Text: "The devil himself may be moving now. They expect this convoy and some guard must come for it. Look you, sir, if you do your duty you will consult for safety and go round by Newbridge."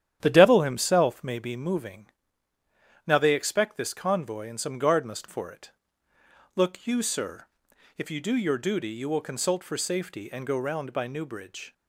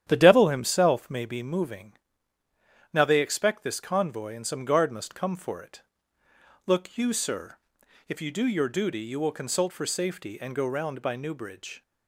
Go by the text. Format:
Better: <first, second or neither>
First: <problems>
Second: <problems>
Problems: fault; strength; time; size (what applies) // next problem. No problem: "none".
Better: second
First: starts louder than the rest; strong; until 1.2 s; 10.5 dB // pauses between "moving" and "now"; at 2.0 s; 1.0 s long // skips "come"; at 5.2 s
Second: starts louder than the rest; strong; until 1.0 s; 10.5 dB // pauses between "moving" and "now"; at 1.9 s; 1.0 s long